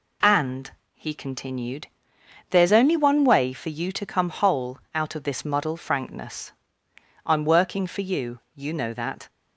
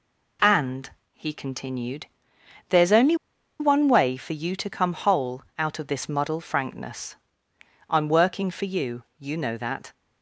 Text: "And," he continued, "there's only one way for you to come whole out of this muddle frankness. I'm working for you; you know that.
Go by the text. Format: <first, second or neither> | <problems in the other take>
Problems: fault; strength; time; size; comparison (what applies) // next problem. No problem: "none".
first | pauses between "only" and "one"; at 3.1 s; 0.45 s long